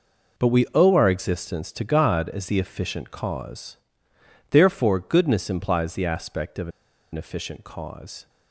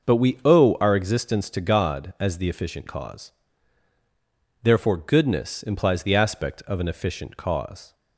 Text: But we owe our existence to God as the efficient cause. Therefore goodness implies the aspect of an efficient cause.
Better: second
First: pauses between "of" and "an"; at 6.6 s; 0.44 s long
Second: none

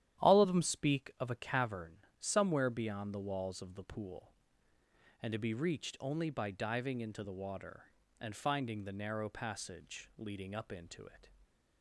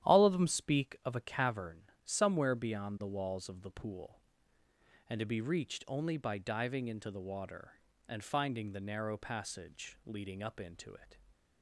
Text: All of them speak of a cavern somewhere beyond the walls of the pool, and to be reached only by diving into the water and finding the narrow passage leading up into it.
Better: neither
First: starts louder than the rest; strong; until 1.3 s; 11 dB // pauses between "cavern" and "somewhere"; slight; at 1.9 s; 0.22 s long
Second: starts louder than the rest; strong; until 1.1 s; 11 dB // pauses between "cavern" and "somewhere"; slight; at 1.8 s; 0.22 s long

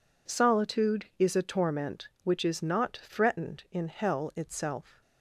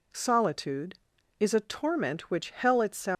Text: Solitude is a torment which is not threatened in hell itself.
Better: first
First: none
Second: skips "is not threatened in"; at 2.4 s

